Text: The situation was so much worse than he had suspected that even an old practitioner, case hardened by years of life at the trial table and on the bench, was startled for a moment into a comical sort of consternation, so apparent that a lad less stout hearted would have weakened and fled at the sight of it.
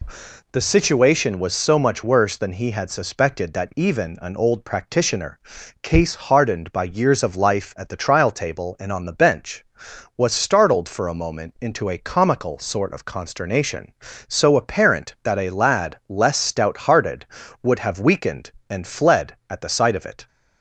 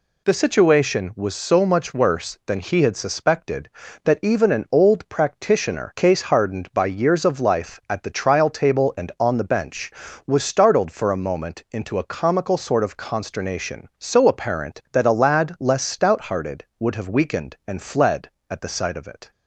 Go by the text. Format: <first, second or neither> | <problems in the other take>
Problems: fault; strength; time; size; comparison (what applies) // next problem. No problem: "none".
neither | none